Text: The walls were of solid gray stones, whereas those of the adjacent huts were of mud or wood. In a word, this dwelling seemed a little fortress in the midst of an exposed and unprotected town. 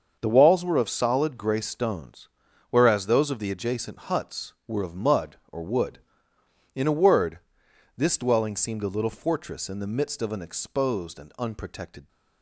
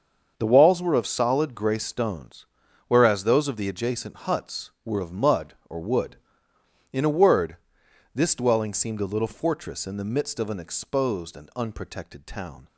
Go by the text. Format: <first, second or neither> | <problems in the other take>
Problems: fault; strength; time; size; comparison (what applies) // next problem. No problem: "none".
second | starts louder than the rest; until 1.2 s; 6.5 dB; also in the second // stops before "town"; at 12.0 s